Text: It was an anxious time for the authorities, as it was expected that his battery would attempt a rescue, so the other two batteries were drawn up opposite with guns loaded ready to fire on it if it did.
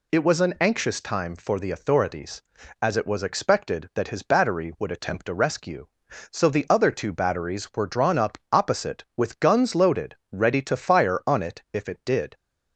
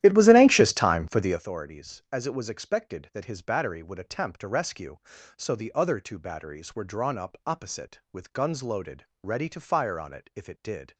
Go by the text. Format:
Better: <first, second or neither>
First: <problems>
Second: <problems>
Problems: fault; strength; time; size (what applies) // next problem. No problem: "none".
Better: first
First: pauses between "loaded" and "ready"; slight; at 10.1 s; 0.16 s long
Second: starts louder than the rest; strong; until 1.4 s; 13 dB // pauses between "loaded" and "ready"; slight; at 9.0 s; 0.18 s long